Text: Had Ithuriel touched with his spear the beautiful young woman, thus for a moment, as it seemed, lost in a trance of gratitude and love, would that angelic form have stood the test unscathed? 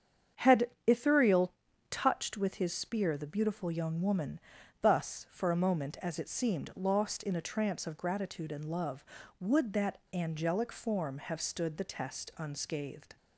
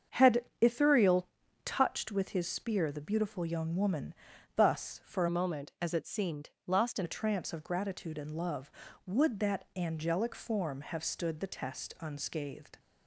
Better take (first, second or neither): first